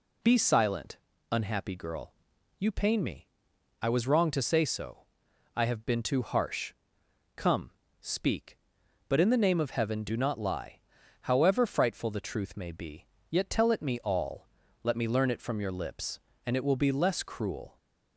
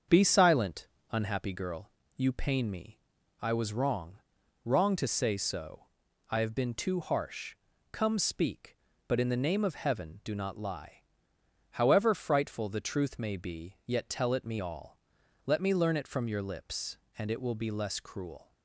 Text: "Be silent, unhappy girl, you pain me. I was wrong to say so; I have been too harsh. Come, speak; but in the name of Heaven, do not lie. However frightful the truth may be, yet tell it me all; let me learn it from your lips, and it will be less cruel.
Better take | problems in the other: first | starts louder than the rest; until 1.3 s; 7 dB // says "wrong" twice; at 4.6 s

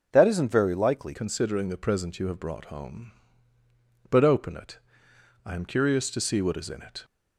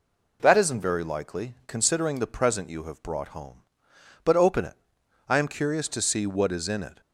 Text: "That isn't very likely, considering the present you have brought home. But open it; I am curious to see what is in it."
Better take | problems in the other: second | changes voice at "considering"; from 1.1 s on; 5.9 s long

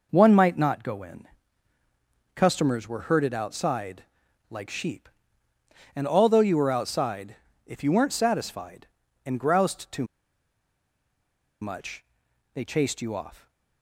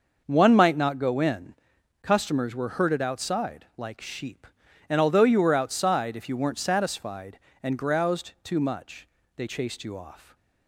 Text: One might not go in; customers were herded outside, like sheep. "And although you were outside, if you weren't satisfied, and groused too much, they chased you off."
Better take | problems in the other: second | pauses between "too" and "much"; strong; at 10.0 s; 1.5 s long

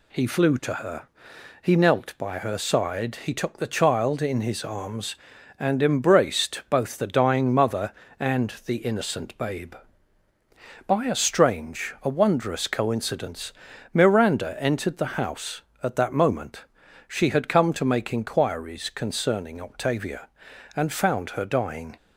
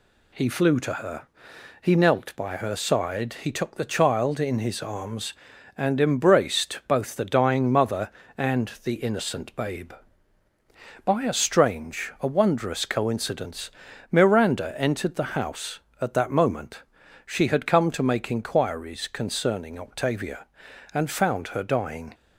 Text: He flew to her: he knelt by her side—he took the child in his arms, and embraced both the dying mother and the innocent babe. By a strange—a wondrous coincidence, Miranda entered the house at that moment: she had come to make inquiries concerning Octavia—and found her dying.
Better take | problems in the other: neither | none

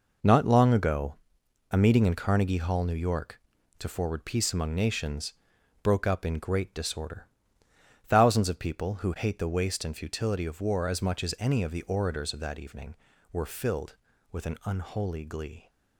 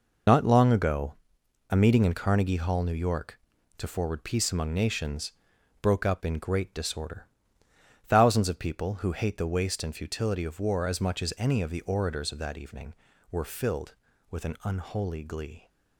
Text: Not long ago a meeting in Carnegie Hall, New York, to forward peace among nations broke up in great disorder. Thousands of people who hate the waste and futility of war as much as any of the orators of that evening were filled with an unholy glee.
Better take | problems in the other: first | loses the start of "Not"; at 0.2 s; 60 ms // pauses between "ago" and "a"; noticeable; at 1.1 s; 0.56 s long; noticeable in the first // pauses between "nations" and "broke"; noticeable; at 5.3 s; 0.48 s long; noticeable in the first

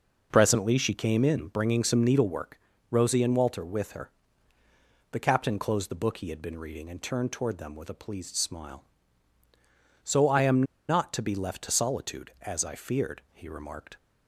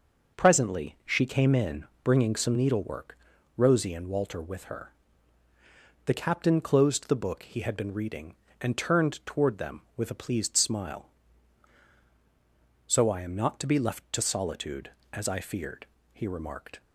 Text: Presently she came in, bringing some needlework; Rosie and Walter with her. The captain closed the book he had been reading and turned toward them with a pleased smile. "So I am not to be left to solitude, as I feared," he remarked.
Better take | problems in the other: second | pauses between "am" and "not"; slight; at 10.6 s; 0.25 s long

